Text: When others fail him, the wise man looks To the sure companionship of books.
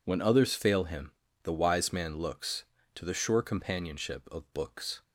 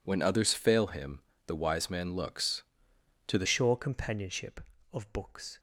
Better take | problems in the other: first | changes voice at "sure"; from 3.4 s on; 2.1 s long

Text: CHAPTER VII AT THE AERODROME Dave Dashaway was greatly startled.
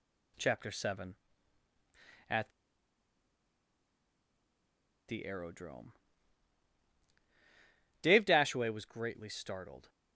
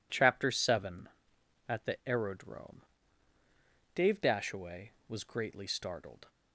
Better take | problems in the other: second | pauses between "AT" and "THE"; strong; at 2.4 s; 2.5 s long // pauses between "AERODROME" and "Dave"; strong; at 5.9 s; 2.0 s long; also in the second

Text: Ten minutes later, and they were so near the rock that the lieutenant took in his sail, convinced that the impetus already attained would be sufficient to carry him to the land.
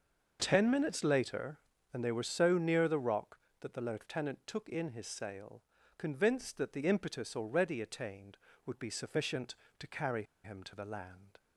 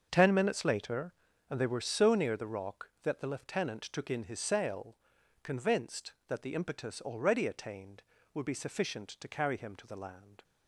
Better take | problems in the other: second | starts louder than the rest; until 1.4 s; 6.5 dB; also in the second // pauses between "carry" and "him"; slight; at 10.2 s; 0.21 s long

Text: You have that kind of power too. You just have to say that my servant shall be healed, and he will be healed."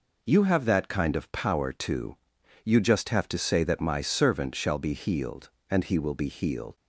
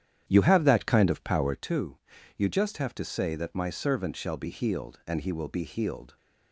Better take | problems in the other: first | starts louder than the rest; strong; until 1.6 s; 10 dB

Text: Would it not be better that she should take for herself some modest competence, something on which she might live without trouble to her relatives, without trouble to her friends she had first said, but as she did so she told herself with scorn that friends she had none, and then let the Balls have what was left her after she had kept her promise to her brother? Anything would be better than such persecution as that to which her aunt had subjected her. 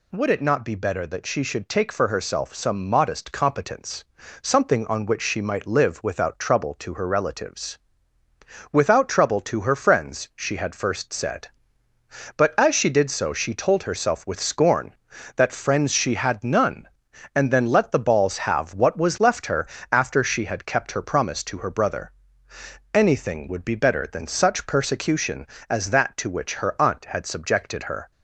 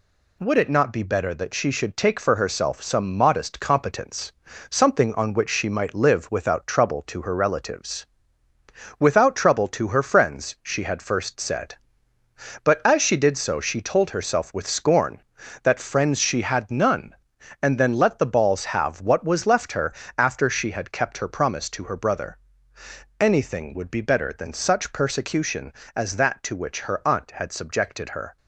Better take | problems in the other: first | gets quieter; throughout; 4 dB // pauses between "her" and "after"; slight; at 19.9 s; 0.24 s long; slight in the first

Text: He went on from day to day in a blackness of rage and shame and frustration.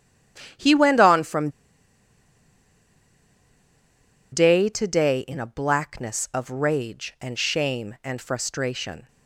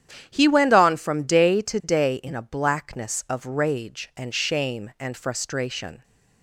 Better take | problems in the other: second | starts louder than the rest; strong; until 4.3 s; 10 dB; strong in the second // pauses between "from" and "day"; strong; at 1.4 s; 2.8 s long

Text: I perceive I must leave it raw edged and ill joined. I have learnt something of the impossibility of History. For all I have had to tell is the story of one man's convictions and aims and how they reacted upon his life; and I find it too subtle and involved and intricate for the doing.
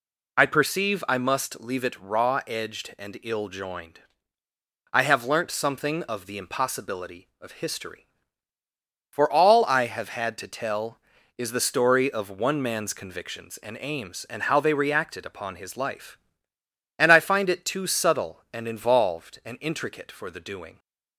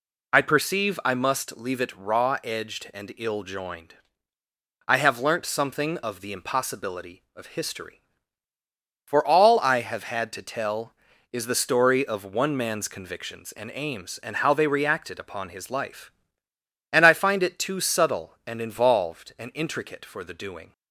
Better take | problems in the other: neither | none

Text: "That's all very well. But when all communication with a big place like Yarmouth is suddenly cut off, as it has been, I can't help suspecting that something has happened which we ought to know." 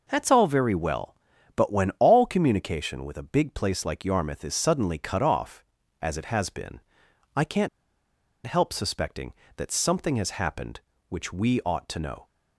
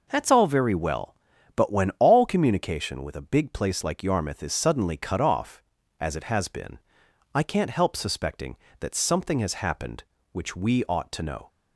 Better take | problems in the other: second | pauses between "can't" and "help"; noticeable; at 7.6 s; 0.78 s long

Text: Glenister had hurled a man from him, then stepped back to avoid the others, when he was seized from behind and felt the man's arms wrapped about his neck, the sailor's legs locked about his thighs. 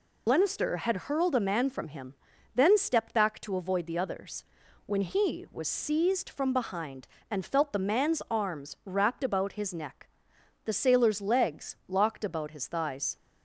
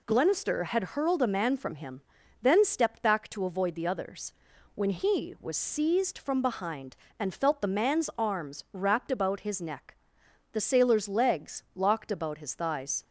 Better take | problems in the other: second | loses the start of "Glenister"; at 0.2 s; 90 ms

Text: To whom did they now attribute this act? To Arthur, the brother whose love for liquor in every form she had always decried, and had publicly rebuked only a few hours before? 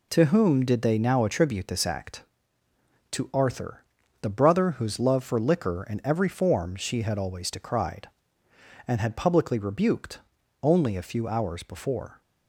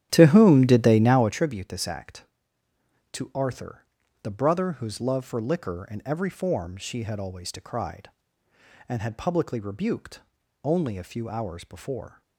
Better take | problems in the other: first | starts louder than the rest; strong; until 1.4 s; 10.5 dB // pauses between "rebuked" and "only"; at 10.1 s; 0.44 s long; also in the first

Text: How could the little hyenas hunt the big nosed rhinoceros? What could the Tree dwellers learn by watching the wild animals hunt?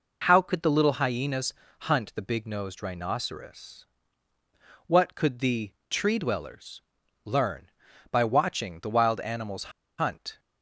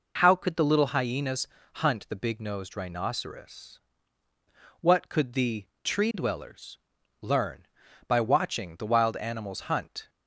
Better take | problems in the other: second | pauses between "hyenas" and "hunt"; at 1.5 s; 0.38 s long; also in the second // pauses between "the" and "Tree"; slight; at 5.7 s; 0.18 s long; slight in the second // pauses between "dwellers" and "learn"; at 6.8 s; 0.44 s long; also in the second // pauses between "animals" and "hunt"; slight; at 9.7 s; 0.29 s long

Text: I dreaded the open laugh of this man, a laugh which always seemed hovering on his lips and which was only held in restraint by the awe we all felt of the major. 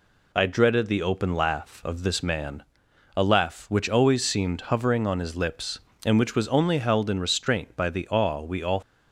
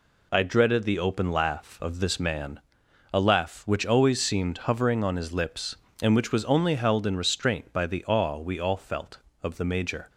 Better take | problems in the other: second | stops before "felt of the major"; at 8.8 s

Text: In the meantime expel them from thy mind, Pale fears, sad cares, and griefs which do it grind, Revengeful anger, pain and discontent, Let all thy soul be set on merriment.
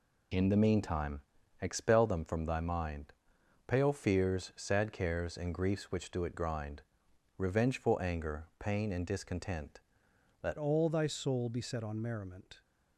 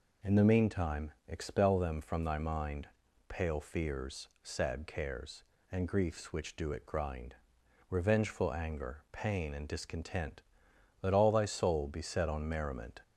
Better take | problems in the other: second | pauses between "meantime" and "expel"; at 1.2 s; 0.40 s long; slight in the second // changes voice at "all"; from 10.5 s on; 2.1 s long

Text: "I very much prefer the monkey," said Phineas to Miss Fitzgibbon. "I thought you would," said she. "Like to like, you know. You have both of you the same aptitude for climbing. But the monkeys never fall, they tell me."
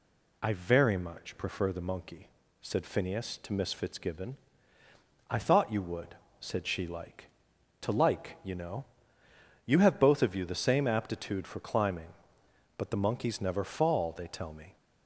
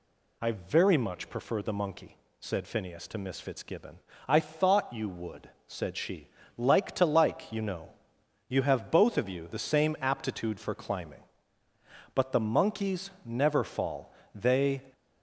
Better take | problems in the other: first | stops before "tell me"; at 14.9 s

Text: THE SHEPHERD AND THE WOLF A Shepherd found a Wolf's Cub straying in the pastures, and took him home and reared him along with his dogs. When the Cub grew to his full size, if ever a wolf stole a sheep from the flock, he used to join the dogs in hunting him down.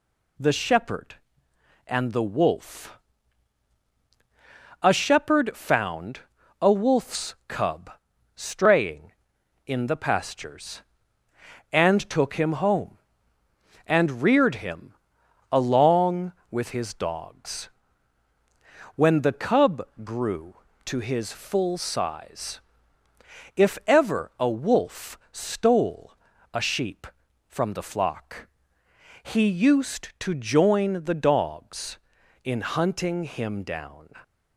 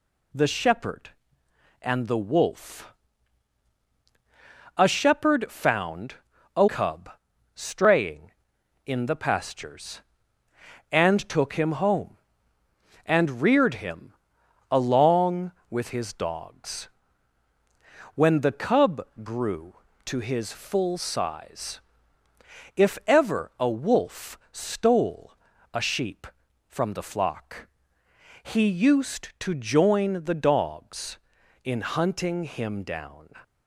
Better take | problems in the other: first | pauses between "WOLF" and "A"; strong; at 2.9 s; 1.8 s long; strong in the first // pauses between "found" and "a"; at 6.1 s; 0.42 s long; also in the first // skips "Wolf's"; at 6.6 s // pauses between "Cub" and "straying"; at 7.0 s; 0.44 s long; also in the first // pauses between "him" and "along"; noticeable; at 14.1 s; 0.58 s long; noticeable in the first // pauses between "Cub" and "grew"; slight; at 19.0 s; 0.18 s long; slight in the first // pauses between "stole" and "a"; at 25.3 s; 0.38 s long; also in the first

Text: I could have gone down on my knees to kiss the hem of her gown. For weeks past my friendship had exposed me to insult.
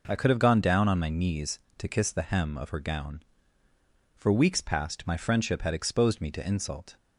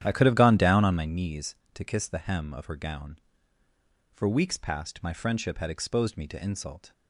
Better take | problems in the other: first | starts louder than the rest; strong; until 1.2 s; 10.5 dB

